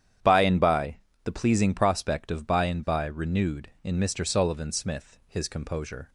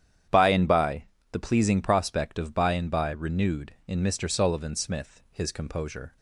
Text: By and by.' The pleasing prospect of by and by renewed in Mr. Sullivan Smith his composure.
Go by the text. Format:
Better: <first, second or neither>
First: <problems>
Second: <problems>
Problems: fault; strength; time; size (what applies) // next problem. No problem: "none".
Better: neither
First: starts louder than the rest; strong; until 1.5 s; 9.5 dB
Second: starts louder than the rest; strong; until 1.5 s; 9.5 dB